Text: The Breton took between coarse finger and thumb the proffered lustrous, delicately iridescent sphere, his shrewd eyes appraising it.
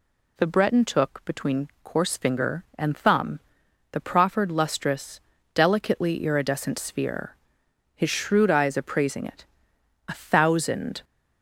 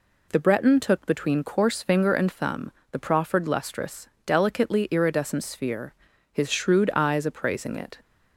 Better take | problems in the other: second | pauses between "thumb" and "the"; noticeable; at 3.3 s; 0.52 s long; slight in the second // goes on to say "A thousand"; noticeable; from 10.0 s on; 0.94 s long

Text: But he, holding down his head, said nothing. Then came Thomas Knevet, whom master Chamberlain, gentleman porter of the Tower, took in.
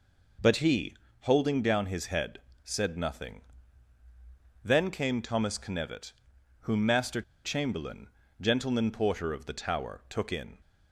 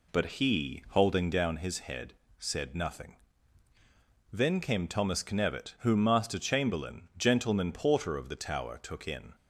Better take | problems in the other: second | pauses between "master" and "Chamberlain"; slight; at 7.2 s; 0.23 s long

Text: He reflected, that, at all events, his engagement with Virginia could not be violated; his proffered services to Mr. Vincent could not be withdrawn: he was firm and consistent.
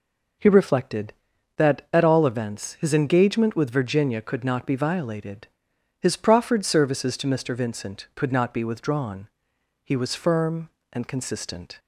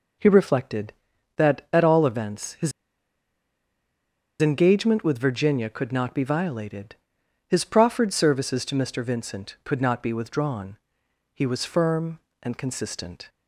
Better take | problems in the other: first | pauses between "his" and "engagement"; strong; at 2.7 s; 1.7 s long

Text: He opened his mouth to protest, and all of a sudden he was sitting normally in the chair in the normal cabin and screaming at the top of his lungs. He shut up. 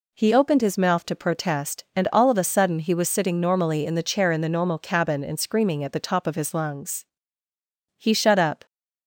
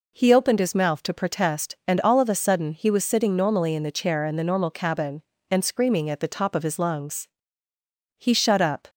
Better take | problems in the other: neither | none

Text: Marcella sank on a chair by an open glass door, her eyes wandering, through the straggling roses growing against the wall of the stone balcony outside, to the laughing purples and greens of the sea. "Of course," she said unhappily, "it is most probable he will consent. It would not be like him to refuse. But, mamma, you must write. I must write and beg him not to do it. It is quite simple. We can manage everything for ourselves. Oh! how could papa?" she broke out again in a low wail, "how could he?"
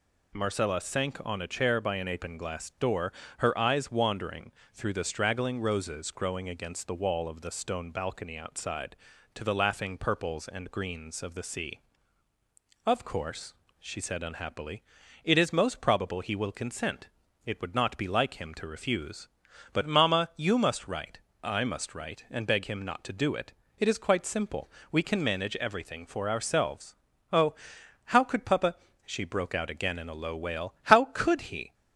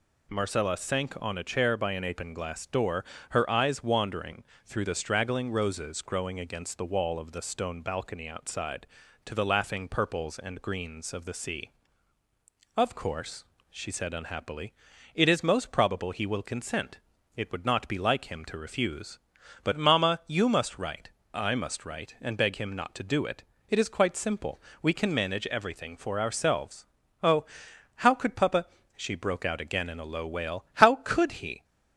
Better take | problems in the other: neither | none

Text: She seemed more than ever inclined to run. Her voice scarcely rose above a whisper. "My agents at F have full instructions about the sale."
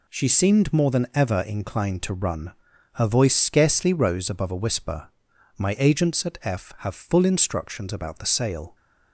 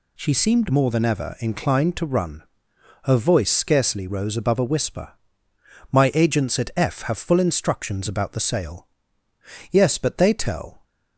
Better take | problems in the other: first | goes on to say "Yes but they tell"; noticeable; from 9.7 s on; 1.1 s long

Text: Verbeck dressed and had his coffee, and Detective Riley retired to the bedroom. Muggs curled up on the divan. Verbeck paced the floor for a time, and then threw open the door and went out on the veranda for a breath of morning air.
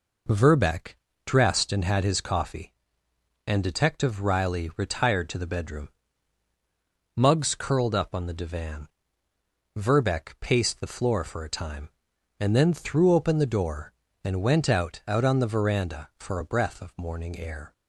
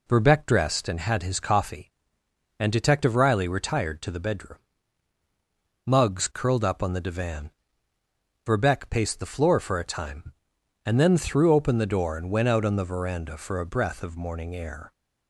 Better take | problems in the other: second | pauses between "Verbeck" and "dressed"; slight; at 0.9 s; 0.28 s long // says "out" twice; at 15.0 s

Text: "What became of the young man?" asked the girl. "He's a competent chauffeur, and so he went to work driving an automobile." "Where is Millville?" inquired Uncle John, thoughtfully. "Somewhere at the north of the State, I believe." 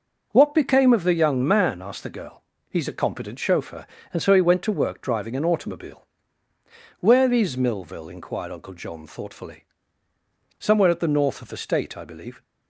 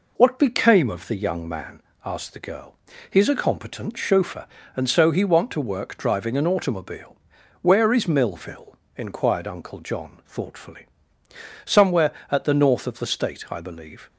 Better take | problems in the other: first | says "want" for "went"; at 5.2 s

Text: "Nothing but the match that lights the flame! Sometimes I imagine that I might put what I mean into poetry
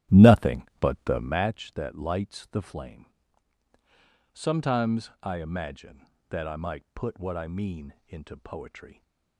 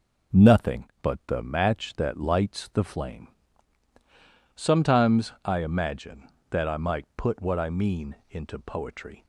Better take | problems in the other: second | starts louder than the rest; strong; until 1.5 s; 12 dB // pauses between "mean" and "into"; slight; at 7.9 s; 0.16 s long; slight in the second

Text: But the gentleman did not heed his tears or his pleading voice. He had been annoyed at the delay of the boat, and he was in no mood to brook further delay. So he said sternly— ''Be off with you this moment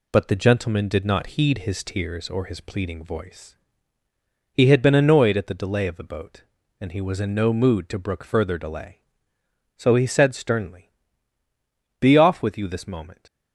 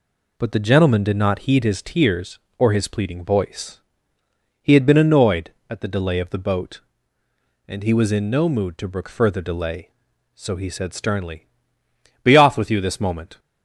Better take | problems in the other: neither | none

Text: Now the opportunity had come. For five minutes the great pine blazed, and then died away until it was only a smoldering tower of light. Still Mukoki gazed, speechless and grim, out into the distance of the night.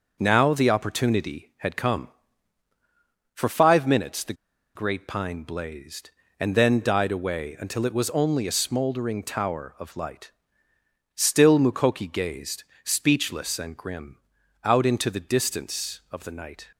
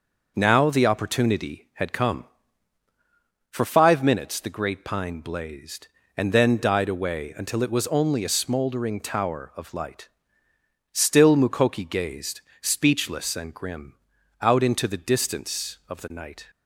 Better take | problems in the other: second | starts louder than the rest; until 1.2 s; 6 dB; also in the second // pauses between "the" and "great"; at 4.3 s; 0.41 s long

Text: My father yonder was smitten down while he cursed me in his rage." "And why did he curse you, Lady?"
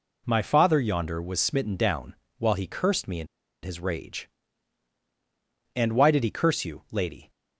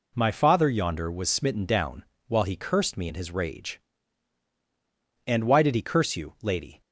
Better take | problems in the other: second | pauses between "down" and "while"; slight; at 2.1 s; 0.22 s long; slight in the second // pauses between "in" and "his"; at 3.2 s; 0.36 s long

